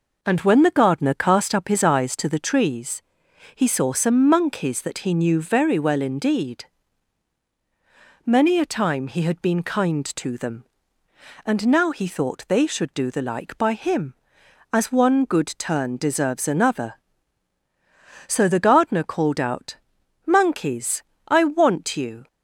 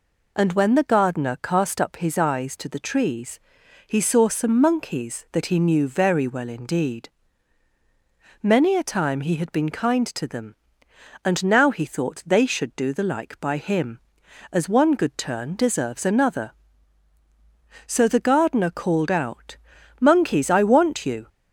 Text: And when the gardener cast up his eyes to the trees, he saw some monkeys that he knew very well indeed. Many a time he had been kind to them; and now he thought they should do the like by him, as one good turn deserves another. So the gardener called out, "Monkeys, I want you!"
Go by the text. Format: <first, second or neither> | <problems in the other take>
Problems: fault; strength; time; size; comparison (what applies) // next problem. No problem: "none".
neither | none